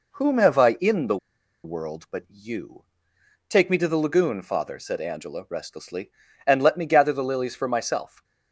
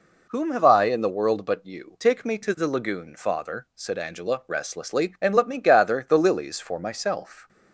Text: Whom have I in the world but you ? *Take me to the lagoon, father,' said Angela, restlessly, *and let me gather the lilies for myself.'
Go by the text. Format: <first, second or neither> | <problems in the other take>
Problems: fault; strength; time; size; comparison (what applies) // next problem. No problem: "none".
second | pauses between "the" and "world"; noticeable; at 1.1 s; 0.47 s long